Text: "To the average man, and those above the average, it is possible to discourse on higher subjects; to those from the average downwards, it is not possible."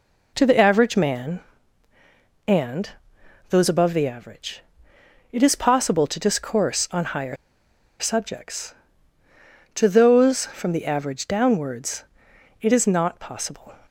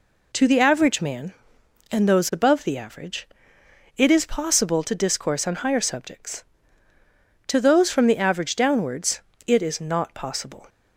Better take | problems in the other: second | pauses between "and" and "those"; noticeable; at 2.8 s; 0.60 s long // pauses between "higher" and "subjects"; noticeable; at 7.3 s; 0.63 s long

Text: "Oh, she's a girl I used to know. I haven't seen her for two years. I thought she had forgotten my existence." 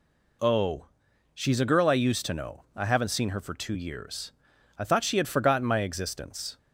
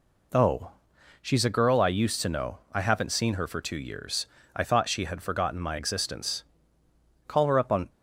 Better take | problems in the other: first | goes on to say "Call her up on"; noticeable; from 7.2 s on; 0.62 s long

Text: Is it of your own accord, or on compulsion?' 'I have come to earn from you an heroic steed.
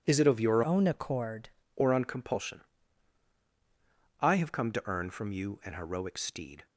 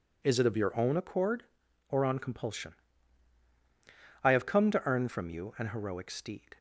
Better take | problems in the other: second | changes voice from "own" to "accord"; from 0.6 to 1.4 s; 0.8 s long

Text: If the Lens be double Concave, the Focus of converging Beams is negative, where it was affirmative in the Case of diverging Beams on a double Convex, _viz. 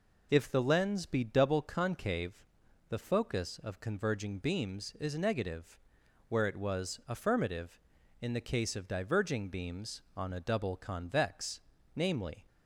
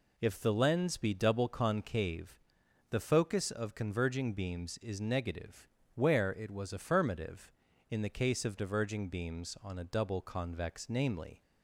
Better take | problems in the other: neither | none

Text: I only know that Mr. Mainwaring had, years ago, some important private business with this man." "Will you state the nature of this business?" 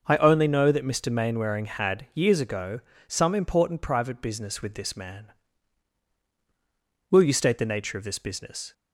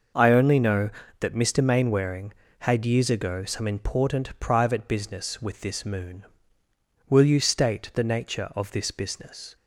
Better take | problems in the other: first | says "moon" for "man"; at 5.8 s

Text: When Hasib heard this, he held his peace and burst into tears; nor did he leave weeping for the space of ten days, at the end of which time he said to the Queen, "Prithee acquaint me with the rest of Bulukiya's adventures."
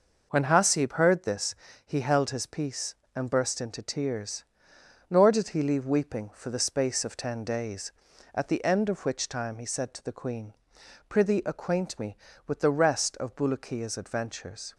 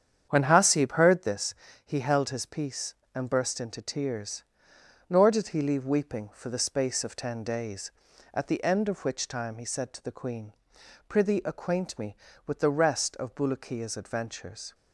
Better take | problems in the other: first | starts louder than the rest; strong; until 1.3 s; 8.5 dB

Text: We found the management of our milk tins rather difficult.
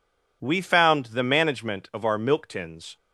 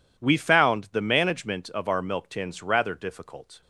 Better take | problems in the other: second | stops before "rather difficult"; at 2.9 s

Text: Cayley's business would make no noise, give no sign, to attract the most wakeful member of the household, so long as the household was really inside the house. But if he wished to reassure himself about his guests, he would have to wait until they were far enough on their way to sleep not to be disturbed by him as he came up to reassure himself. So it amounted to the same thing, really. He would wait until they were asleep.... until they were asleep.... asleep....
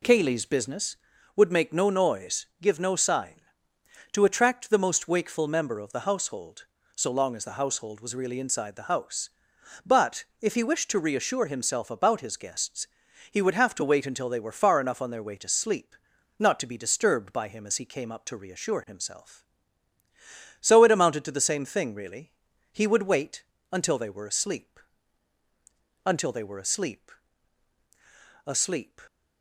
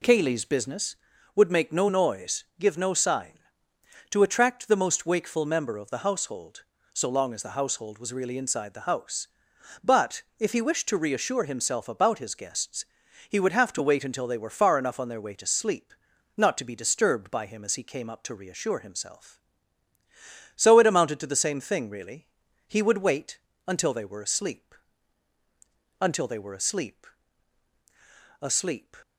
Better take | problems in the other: neither | pauses between "But" and "if"; slight; the same in both // pauses between "sleep" and "not"; the same in both // pauses between "wait" and "until"; slight; the same in both

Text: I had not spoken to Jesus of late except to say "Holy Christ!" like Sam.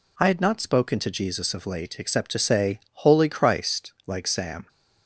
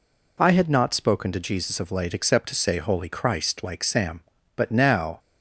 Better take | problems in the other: first | goes on to say "But now"; noticeable; from 4.5 s on; 0.64 s long

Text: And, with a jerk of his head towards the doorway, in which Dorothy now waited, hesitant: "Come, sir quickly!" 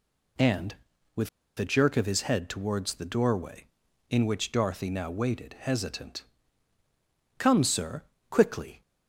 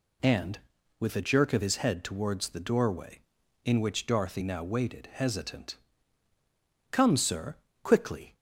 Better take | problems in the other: second | pauses between "with" and "a"; slight; at 1.2 s; 0.30 s long // pauses between "sir" and "quickly"; slight; at 8.0 s; 0.26 s long; slight in the second

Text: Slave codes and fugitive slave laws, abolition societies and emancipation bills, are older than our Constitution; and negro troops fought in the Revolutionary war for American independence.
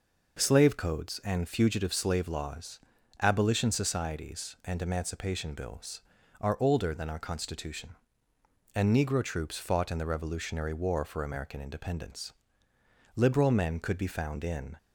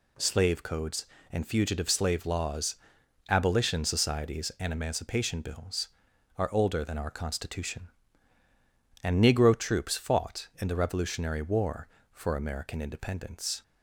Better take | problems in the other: second | goes on to say "Liberal men could be found in"; from 13.1 s on; 1.6 s long

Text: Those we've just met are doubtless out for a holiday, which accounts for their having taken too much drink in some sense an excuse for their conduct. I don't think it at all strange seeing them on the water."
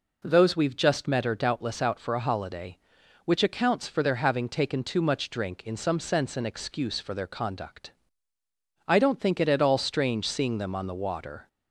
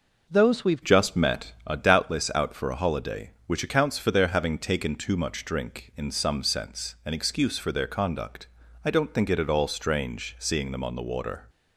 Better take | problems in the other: first | changes voice at "just"; from 0.8 s on; 10.6 s long

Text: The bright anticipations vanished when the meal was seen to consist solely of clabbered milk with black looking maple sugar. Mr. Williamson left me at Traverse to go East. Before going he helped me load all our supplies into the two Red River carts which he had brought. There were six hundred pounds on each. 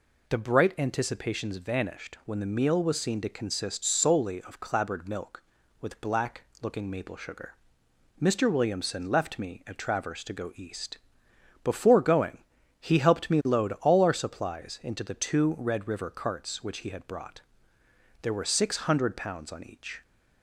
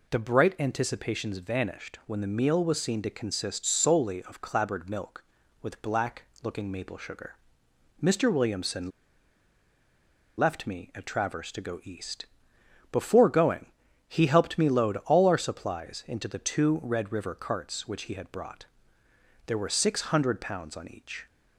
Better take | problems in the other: first | pauses between "black" and "looking"; slight; at 6.2 s; 0.20 s long; slight in the first // pauses between "Williamson" and "left"; strong; at 8.8 s; 1.4 s long // pauses between "going" and "he"; at 13.6 s; 0.42 s long; also in the first

